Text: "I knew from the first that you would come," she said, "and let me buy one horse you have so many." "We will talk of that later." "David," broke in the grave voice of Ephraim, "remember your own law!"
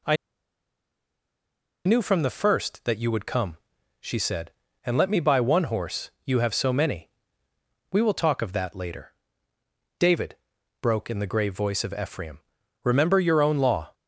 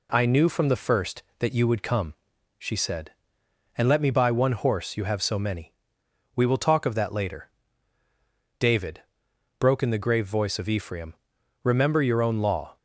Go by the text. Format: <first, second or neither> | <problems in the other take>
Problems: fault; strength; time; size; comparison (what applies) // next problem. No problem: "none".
second | pauses between "I" and "knew"; strong; at 0.1 s; 1.6 s long // pauses between "horse" and "you"; slight; at 6.0 s; 0.16 s long